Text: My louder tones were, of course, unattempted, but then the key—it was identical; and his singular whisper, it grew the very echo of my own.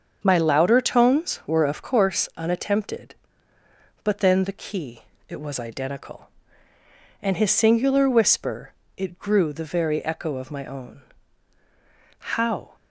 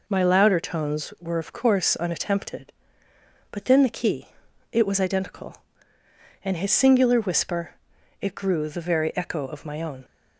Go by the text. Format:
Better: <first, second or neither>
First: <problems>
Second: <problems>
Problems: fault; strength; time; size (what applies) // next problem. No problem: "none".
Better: second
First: starts louder than the rest; until 1.2 s; 7 dB // goes on to say "How"; from 12.1 s on; 0.56 s long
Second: none